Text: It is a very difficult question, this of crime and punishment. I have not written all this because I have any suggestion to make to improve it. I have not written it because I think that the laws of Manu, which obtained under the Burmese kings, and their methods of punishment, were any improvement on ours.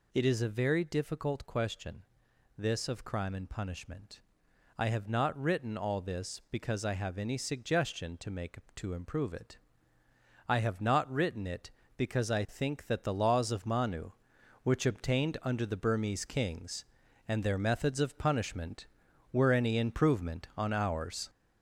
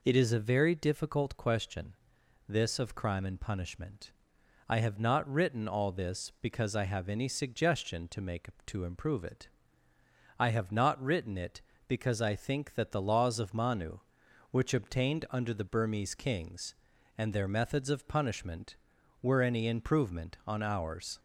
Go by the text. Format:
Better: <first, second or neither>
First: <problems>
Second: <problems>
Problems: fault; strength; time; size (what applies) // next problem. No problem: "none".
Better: second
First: gets louder; noticeable; throughout; 5 dB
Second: none